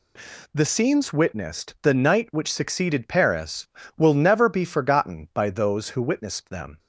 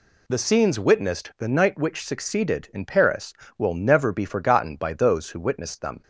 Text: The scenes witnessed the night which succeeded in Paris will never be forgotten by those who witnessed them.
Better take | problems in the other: second | skips "in"; at 3.0 s

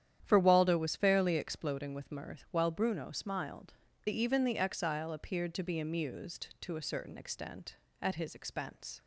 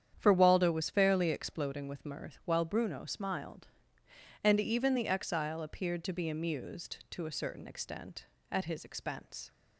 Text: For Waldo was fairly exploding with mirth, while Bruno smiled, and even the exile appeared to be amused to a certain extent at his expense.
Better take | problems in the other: second | starts louder than the rest; strong; until 1.2 s; 10 dB; strong in the second // skips "and"; at 3.9 s

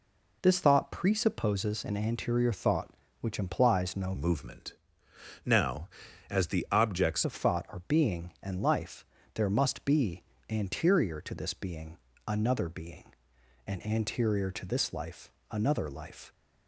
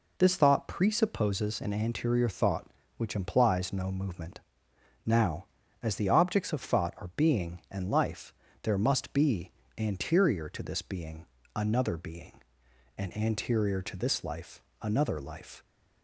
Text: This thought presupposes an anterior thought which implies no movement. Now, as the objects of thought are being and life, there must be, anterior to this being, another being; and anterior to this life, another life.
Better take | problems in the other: second | changes voice from "movement" to "objects"; from 4.1 to 7.2 s; 3.1 s long

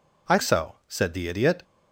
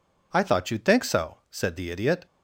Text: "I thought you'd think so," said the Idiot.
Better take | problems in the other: second | skips "thought you'd think"; at 0.3 s

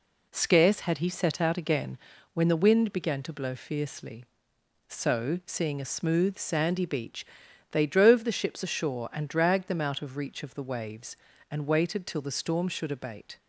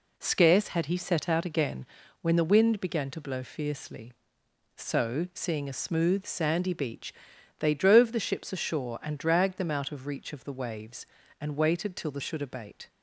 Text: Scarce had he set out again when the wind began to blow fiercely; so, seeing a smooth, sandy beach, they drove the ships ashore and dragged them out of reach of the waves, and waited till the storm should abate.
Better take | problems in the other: first | pauses between "again" and "when"; at 1.8 s; 0.38 s long; also in the first // skips "storm"; at 12.2 s

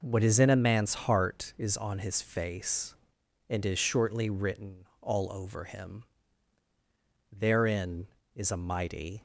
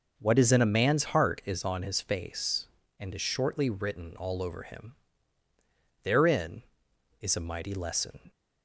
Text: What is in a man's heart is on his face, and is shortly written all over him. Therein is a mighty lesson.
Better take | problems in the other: second | stops before "lesson"; at 9.1 s

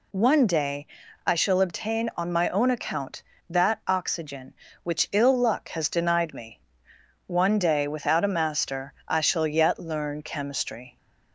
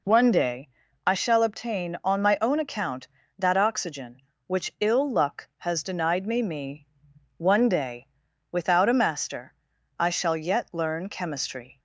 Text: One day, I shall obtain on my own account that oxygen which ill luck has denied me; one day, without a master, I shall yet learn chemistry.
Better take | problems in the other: first | says "me" twice; at 6.4 s

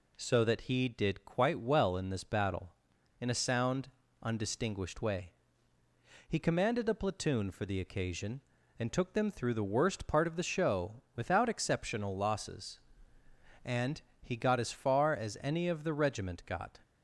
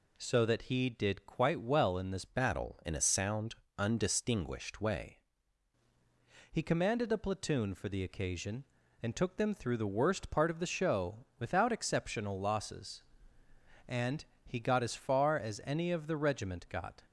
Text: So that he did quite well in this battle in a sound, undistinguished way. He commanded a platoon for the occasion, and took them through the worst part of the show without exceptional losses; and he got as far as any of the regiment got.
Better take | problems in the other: first | changes voice from "battle" to "way"; from 2.2 to 5.1 s; 2.9 s long // pauses between "and" and "he"; slight; at 14.2 s; 0.22 s long; slight in the first

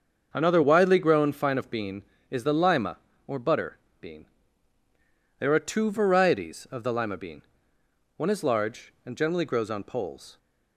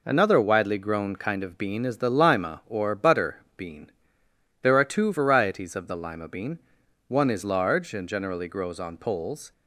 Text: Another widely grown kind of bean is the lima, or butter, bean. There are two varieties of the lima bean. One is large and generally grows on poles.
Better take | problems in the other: second | starts louder than the rest; until 1.3 s; 6.5 dB // says "fine" for "kind"; at 1.3 s

